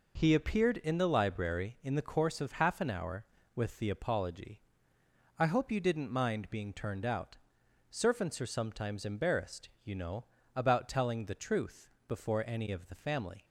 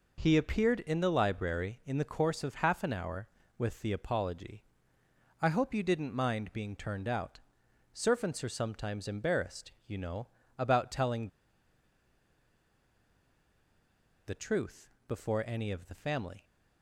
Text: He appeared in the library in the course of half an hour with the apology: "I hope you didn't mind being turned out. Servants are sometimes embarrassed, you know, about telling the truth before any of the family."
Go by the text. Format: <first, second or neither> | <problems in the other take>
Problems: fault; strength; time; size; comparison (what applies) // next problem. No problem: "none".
first | pauses between "telling" and "the"; strong; at 11.2 s; 2.9 s long // pauses between "truth" and "before"; slight; at 14.9 s; 0.18 s long; slight in the first